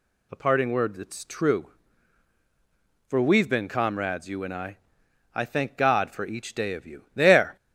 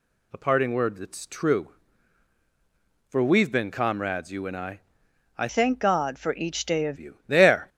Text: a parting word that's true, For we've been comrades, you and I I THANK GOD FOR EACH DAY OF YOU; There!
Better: first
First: pauses between "I" and "I"; noticeable; at 4.7 s; 0.58 s long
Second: pauses between "I" and "I"; noticeable; at 4.8 s; 0.58 s long // changes voice from "THANK" to "OF"; from 5.4 to 6.9 s; 1.5 s long

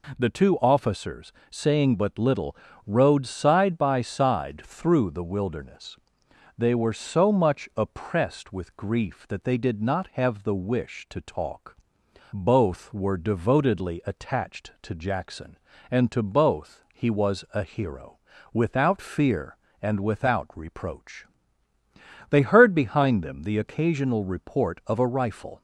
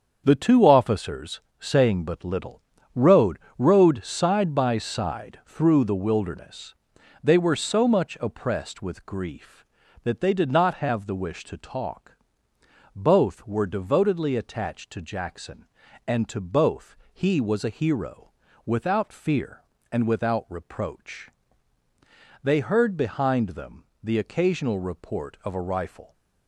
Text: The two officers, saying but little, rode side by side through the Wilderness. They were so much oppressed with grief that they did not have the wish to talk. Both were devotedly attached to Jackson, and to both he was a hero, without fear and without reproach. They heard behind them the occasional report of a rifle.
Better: first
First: none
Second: starts louder than the rest; until 1.2 s; 7 dB // says "rode" twice; at 3.5 s // pauses between "both" and "he"; slight; at 16.9 s; 0.16 s long // pauses between "them" and "the"; slight; at 23.8 s; 0.20 s long

